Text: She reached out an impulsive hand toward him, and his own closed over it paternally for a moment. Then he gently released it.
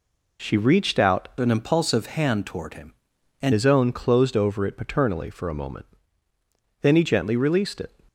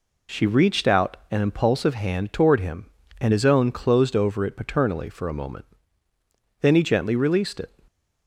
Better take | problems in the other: second | changes voice from "an" to "and"; from 1.3 to 3.5 s; 2.2 s long

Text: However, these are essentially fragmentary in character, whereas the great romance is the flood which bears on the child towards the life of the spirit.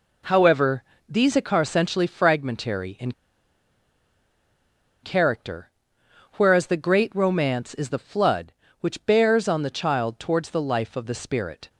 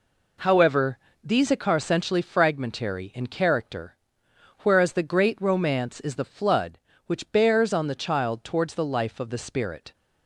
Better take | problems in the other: second | pauses between "in" and "character"; strong; at 3.1 s; 1.9 s long

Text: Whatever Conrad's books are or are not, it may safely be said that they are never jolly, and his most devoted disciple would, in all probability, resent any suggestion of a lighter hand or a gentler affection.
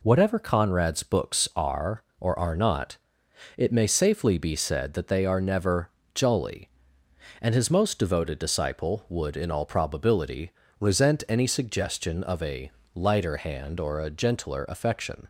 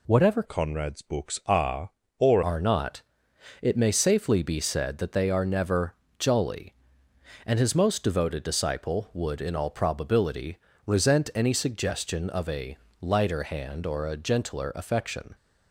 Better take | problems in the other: first | changes voice from "Conrad's" to "or"; from 0.4 to 2.4 s; 2.0 s long // pauses between "never" and "jolly"; slight; at 5.9 s; 0.22 s long; slight in the first // pauses between "a" and "lighter"; slight; at 12.7 s; 0.24 s long; slight in the first

